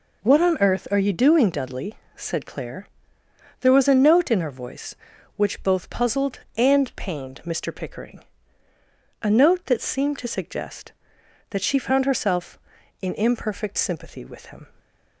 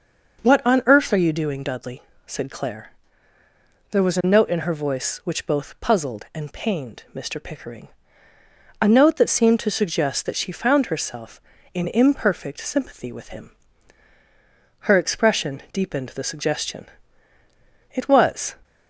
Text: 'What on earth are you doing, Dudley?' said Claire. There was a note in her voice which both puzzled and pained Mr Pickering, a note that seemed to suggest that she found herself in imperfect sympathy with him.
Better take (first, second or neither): first